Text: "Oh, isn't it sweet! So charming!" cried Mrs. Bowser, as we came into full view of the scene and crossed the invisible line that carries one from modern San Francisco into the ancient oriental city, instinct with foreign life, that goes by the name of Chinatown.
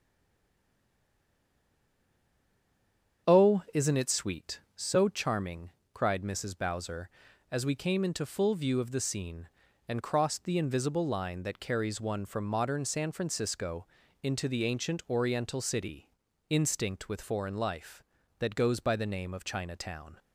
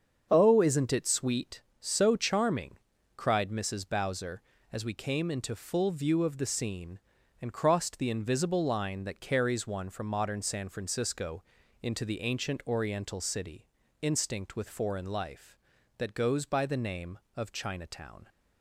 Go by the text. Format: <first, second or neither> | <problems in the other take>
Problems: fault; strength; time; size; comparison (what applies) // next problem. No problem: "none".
second | stays silent before the first word; strong; until 3.2 s; 3.2 s long // starts louder than the rest; strong; until 4.3 s; 7.5 dB; also in the second // pauses between "Francisco" and "into"; slight; at 13.8 s; 0.36 s long; also in the second